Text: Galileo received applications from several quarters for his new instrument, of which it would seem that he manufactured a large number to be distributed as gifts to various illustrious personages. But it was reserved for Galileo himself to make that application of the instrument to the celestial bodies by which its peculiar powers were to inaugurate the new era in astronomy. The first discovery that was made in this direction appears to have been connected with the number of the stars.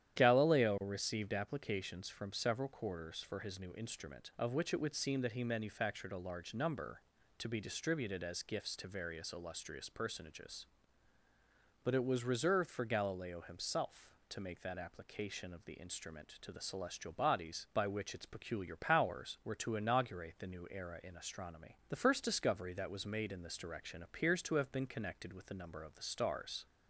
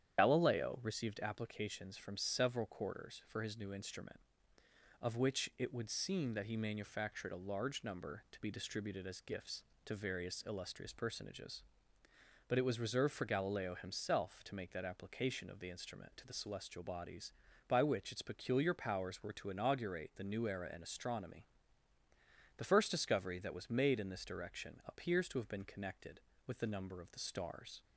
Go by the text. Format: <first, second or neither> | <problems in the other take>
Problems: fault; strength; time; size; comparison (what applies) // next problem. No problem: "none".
first | loses the start of "Galileo"; at 0.1 s; 95 ms // starts louder than the rest; strong; until 1.2 s; 9.5 dB; strong in the first